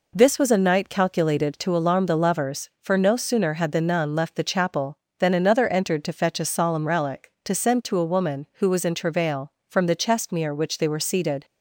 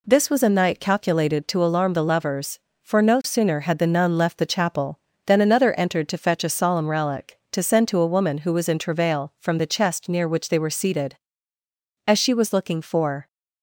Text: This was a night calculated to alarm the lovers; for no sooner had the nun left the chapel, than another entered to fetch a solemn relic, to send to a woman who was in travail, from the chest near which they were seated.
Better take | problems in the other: first | goes on to say "As she was looking for"; noticeable; from 12.0 s on; 1.2 s long

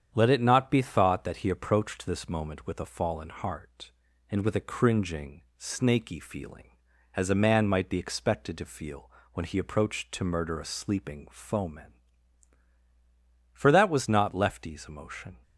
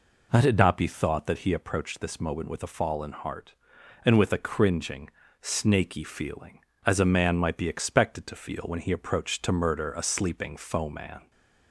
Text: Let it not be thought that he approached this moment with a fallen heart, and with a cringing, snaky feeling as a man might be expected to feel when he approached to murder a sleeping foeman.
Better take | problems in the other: second | starts louder than the rest; strong; until 1.1 s; 8.5 dB // pauses between "feel" and "when"; slight; at 9.1 s; 0.24 s long // goes on to say "For that was not Lefty's emotion"; strong; from 13.5 s on; 1.9 s long

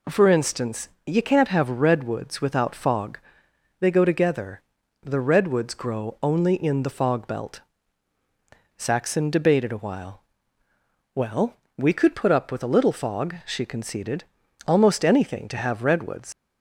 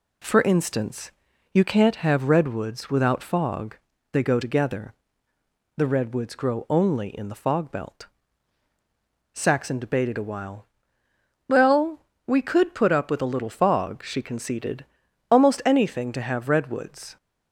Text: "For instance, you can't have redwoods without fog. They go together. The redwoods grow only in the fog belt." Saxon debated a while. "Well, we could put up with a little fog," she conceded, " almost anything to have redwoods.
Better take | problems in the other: second | leaves "redwoods" unfinished; at 16.3 s; 100 ms

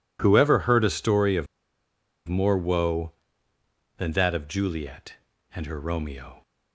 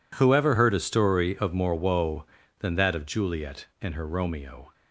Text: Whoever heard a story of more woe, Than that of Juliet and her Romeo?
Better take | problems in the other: second | pauses between "of" and "more"; noticeable; at 1.4 s; 0.81 s long

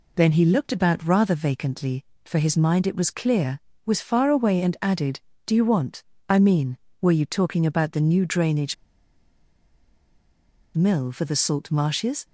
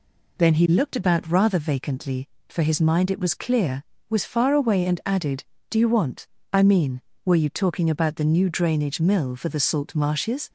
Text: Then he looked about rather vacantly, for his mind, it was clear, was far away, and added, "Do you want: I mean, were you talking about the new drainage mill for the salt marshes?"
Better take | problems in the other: second | pauses between "drainage" and "mill"; strong; at 8.7 s; 2.0 s long

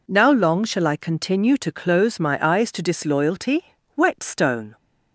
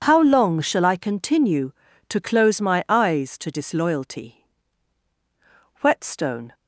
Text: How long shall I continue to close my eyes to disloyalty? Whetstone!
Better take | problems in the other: second | says "Now" for "How"; at 0.0 s

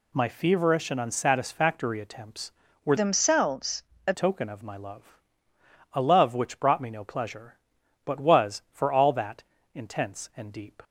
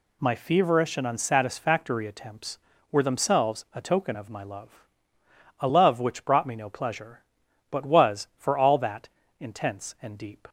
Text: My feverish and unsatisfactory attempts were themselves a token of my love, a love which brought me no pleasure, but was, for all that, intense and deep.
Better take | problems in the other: second | changes voice from "themselves" to "a"; from 2.9 to 4.1 s; 1.2 s long // pauses between "themselves" and "a"; slight; at 3.8 s; 0.24 s long

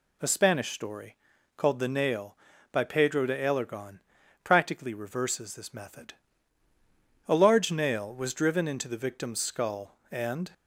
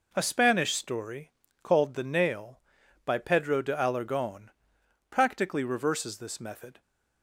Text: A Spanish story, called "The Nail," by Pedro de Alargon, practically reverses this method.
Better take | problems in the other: second | goes on to say "A large nail was driven into the victim's skull and"; strong; from 7.2 s on; 3.2 s long

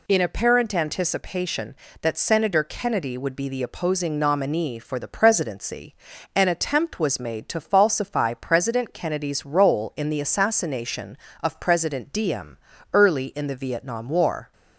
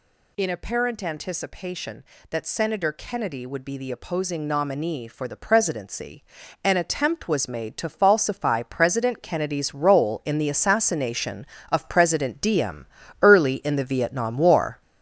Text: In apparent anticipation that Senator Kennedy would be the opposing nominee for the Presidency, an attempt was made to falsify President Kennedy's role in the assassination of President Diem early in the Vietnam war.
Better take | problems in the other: first | gets louder; throughout; 6.5 dB // pauses between "Diem" and "early"; at 12.8 s; 0.38 s long; also in the first

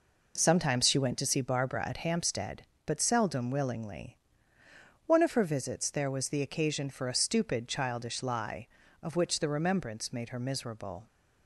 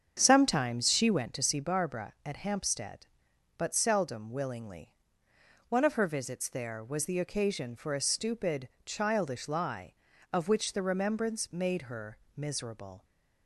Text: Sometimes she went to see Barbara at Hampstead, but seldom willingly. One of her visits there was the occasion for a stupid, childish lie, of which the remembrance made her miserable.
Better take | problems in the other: first | starts louder than the rest; strong; until 1.3 s; 7.5 dB // pauses between "her" and "miserable"; slight; at 12.1 s; 0.18 s long

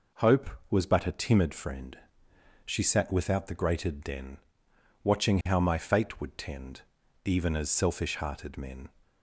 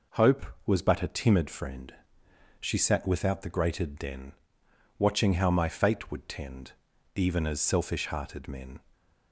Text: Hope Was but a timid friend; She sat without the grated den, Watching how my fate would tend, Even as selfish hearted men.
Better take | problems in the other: neither | none

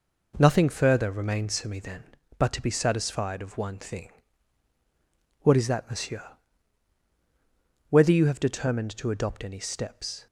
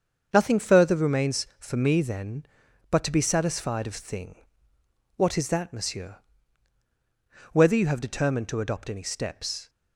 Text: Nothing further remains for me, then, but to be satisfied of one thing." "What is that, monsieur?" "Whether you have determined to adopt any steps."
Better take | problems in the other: first | starts louder than the rest; until 1.3 s; 7 dB // skips "one"; at 3.9 s

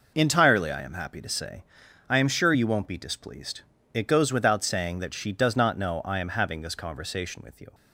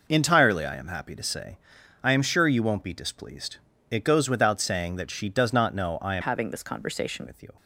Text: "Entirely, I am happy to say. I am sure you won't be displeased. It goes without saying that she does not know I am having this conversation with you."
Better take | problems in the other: first | changes voice from "having" to "conversation"; from 6.2 to 7.2 s; 1.0 s long

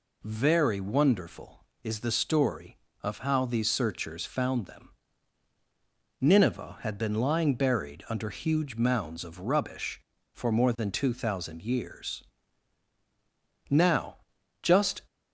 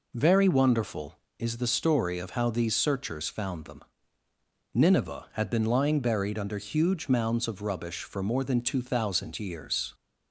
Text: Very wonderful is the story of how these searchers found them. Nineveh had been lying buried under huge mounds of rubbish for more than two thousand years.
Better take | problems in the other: second | goes on to say "Now just"; from 13.6 s on; 1.3 s long

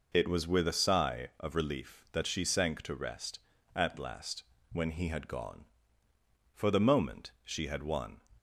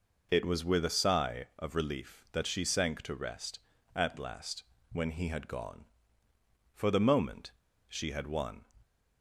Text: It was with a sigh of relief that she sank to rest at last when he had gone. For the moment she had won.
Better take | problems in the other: first | pauses between "last" and "when"; slight; at 4.6 s; 0.30 s long; slight in the first // pauses between "moment" and "she"; at 7.4 s; 0.38 s long

